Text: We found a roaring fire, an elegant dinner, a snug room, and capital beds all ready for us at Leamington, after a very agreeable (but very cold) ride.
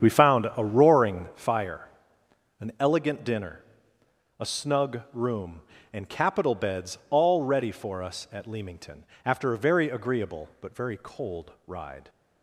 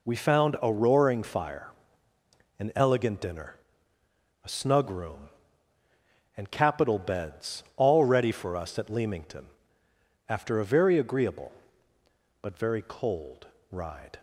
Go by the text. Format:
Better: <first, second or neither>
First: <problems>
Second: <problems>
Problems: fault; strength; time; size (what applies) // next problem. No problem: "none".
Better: second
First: starts louder than the rest; strong; until 1.3 s; 8.5 dB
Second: none